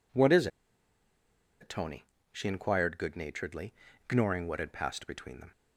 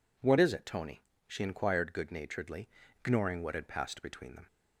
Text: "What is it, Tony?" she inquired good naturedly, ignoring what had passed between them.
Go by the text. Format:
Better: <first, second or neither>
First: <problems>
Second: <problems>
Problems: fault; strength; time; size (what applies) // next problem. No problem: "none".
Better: second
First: pauses between "is" and "it"; at 0.4 s; 1.1 s long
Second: none